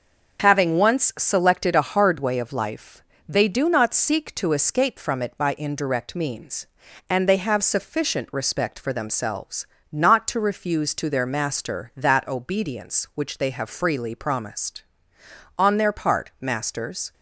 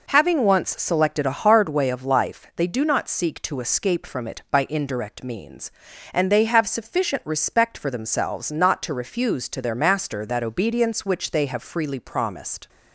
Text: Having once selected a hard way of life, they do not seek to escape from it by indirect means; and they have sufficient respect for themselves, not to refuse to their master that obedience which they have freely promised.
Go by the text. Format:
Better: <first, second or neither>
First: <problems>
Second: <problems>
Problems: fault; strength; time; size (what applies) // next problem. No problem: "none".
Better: second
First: starts louder than the rest; noticeable; until 1.4 s; 6 dB // goes on to say "On their part masters"; from 15.5 s on; 1.5 s long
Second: none